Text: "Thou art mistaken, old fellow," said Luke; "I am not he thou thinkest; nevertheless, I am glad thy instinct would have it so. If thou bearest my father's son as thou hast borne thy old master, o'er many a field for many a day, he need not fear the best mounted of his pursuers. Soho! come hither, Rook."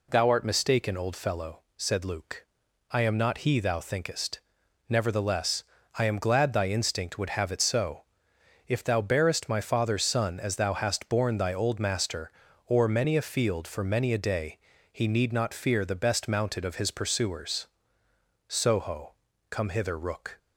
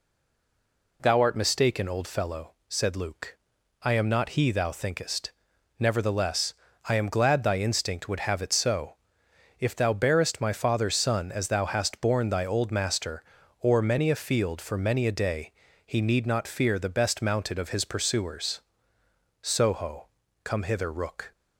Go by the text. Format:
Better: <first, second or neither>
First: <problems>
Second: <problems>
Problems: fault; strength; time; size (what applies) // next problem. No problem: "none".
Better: first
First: none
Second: stays silent before the first word; until 0.9 s; 0.9 s long